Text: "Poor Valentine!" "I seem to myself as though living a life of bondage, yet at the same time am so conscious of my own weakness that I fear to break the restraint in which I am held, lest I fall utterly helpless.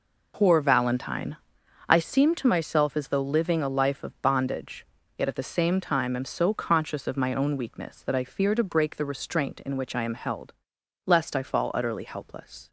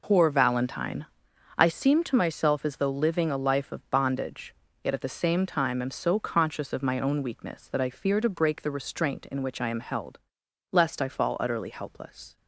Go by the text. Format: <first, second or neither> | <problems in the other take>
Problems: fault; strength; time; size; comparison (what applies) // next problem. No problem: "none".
neither | none